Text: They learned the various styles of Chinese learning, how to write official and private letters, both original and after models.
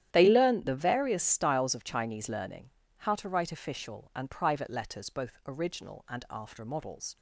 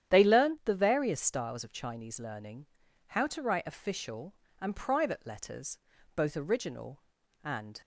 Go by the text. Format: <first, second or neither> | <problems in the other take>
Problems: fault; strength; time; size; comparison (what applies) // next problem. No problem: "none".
first | starts louder than the rest; strong; until 1.1 s; 10 dB; strong in the first // stops before "after models"; at 7.8 s